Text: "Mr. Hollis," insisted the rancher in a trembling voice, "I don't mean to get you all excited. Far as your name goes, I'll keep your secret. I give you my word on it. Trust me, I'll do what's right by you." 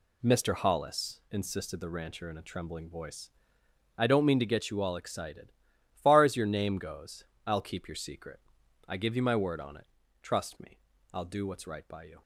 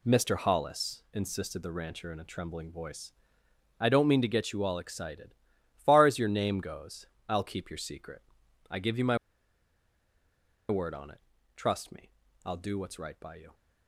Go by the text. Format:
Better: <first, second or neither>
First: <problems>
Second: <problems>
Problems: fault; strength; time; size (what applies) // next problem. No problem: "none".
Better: first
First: none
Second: pauses between "my" and "word"; strong; at 9.1 s; 1.5 s long